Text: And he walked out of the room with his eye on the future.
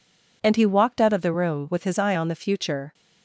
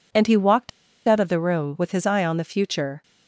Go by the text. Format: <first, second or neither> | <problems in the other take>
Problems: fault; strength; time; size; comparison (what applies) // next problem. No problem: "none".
first | pauses between "walked" and "out"; at 0.6 s; 0.38 s long